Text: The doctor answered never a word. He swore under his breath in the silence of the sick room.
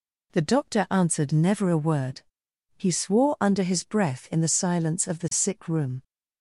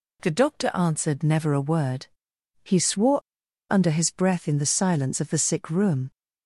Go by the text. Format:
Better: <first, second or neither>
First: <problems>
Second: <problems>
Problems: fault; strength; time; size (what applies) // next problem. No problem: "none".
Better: first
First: none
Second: pauses between "swore" and "under"; noticeable; at 3.1 s; 0.51 s long